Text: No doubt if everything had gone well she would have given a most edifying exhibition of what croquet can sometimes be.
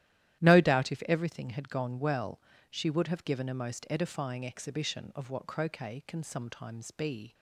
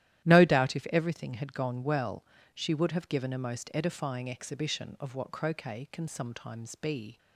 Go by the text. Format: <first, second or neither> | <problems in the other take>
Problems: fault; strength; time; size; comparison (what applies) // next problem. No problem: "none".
neither | starts louder than the rest; strong; the same in both // pauses between "well" and "she"; slight; the same in both